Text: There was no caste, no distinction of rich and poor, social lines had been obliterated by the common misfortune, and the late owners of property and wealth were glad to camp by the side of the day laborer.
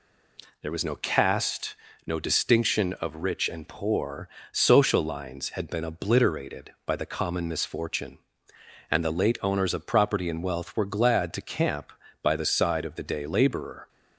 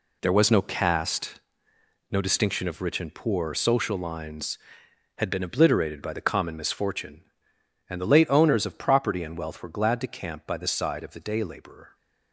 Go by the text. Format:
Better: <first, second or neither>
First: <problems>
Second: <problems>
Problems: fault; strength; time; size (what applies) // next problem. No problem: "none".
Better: first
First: none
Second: gets quieter; strong; throughout; 9.5 dB